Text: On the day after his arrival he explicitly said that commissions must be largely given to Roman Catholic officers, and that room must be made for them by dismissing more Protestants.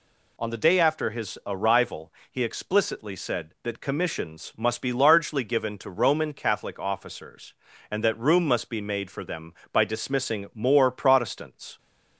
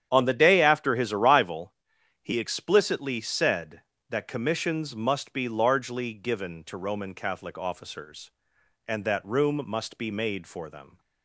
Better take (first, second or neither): first